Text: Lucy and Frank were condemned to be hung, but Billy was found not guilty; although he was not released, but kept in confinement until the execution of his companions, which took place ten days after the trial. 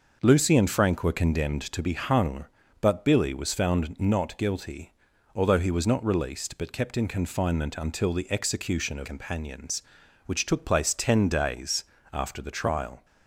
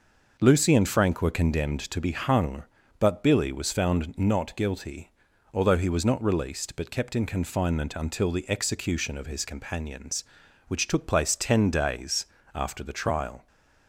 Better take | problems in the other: second | skips "his"; at 9.0 s // pauses between "days" and "after"; slight; at 11.8 s; 0.26 s long; slight in the second

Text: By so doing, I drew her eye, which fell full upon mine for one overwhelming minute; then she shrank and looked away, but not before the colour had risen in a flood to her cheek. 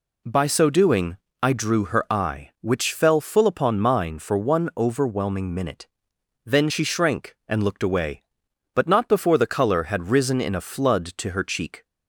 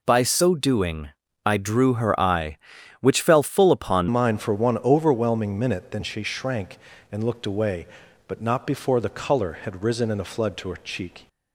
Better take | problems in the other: first | changes voice at "mine"; from 4.0 s on; 7.2 s long

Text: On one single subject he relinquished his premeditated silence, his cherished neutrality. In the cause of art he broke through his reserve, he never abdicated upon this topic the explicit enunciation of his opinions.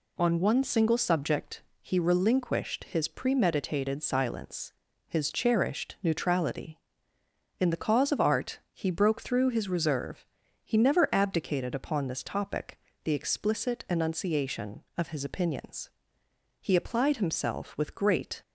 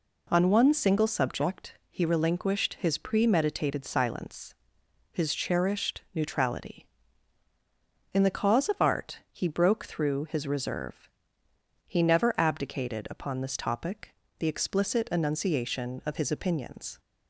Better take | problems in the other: second | pauses between "subject" and "he"; slight; at 1.6 s; 0.18 s long // pauses between "topic" and "the"; slight; at 12.7 s; 0.26 s long; slight in the second // goes on to say "He applied himself with great"; strong; from 16.5 s on; 1.8 s long

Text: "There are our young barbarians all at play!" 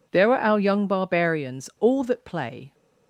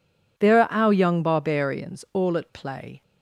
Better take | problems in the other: second | says "that" for "at"; at 2.0 s

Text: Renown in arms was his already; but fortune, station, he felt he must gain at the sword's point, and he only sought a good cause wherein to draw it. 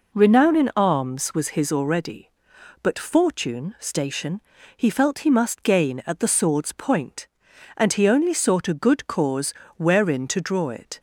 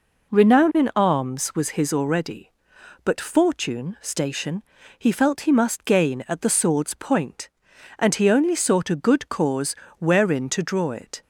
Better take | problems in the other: neither | pauses between "cause" and "wherein"; slight; the same in both

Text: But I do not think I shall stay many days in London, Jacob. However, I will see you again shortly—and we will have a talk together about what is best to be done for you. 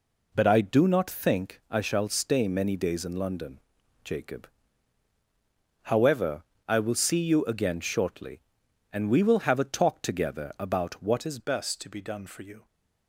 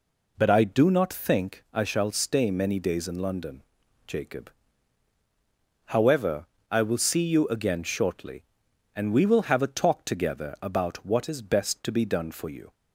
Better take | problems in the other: second | changes voice at "best"; from 11.3 s on; 1.3 s long

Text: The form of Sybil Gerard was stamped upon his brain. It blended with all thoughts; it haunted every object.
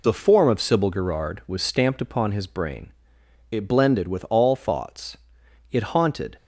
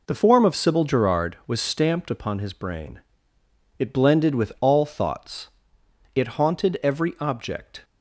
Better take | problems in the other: second | stops before "every object"; at 6.3 s

